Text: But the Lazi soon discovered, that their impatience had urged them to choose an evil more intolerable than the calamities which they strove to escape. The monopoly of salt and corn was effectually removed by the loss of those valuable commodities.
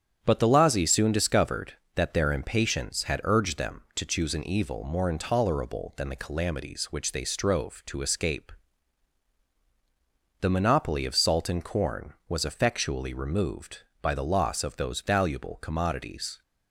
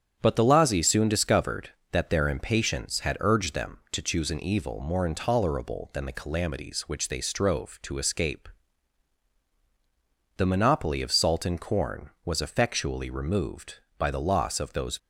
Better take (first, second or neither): first